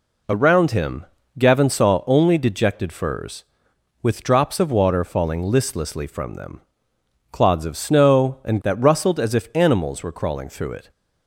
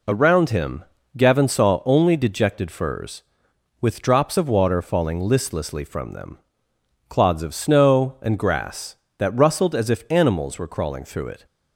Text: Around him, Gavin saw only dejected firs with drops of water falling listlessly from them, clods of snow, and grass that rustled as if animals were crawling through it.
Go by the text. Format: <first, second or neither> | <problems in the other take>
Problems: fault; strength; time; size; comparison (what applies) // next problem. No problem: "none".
second | skips "grass"; at 8.6 s